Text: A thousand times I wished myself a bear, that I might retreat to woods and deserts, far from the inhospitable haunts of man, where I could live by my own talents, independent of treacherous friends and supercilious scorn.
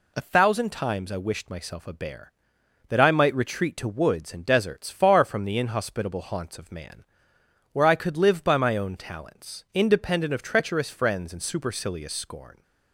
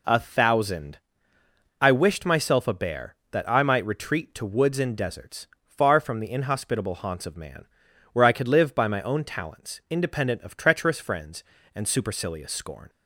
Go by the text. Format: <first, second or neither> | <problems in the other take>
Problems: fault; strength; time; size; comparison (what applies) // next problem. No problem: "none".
first | skips "times"; at 1.4 s